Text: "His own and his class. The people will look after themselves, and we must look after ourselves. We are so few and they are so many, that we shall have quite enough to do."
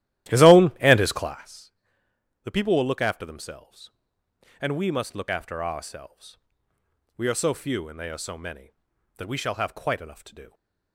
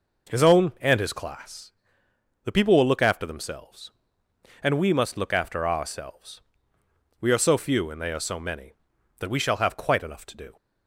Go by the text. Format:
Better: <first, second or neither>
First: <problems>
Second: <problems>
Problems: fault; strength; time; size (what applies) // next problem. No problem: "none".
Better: second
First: starts louder than the rest; strong; until 1.4 s; 14 dB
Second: none